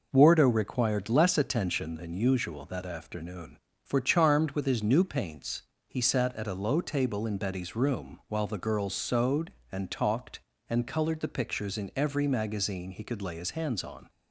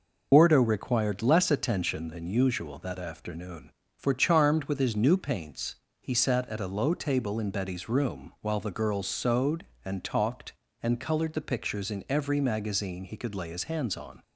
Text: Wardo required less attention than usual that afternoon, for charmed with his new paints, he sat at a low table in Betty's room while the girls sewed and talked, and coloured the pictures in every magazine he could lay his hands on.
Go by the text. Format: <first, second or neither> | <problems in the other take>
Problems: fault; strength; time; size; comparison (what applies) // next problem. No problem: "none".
first | loses the start of "Wardo"; at 0.3 s; 75 ms